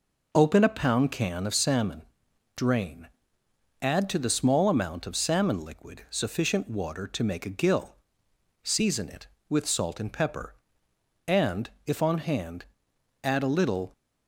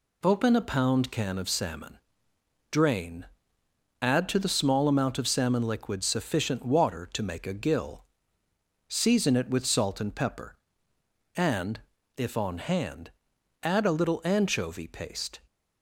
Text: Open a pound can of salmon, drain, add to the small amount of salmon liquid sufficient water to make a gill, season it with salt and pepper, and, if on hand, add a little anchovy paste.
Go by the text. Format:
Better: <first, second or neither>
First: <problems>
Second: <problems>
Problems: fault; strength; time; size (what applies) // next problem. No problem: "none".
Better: second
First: stops before "anchovy paste"; at 13.9 s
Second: none